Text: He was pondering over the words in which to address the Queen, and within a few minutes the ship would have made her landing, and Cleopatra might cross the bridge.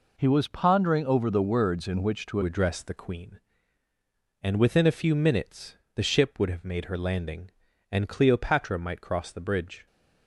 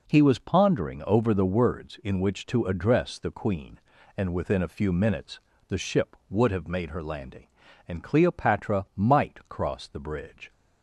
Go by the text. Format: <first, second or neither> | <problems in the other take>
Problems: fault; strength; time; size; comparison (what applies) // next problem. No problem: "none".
second | changes voice at "address"; from 2.4 s on; 7.4 s long // pauses between "minutes" and "the"; slight; at 5.7 s; 0.18 s long; slight in the second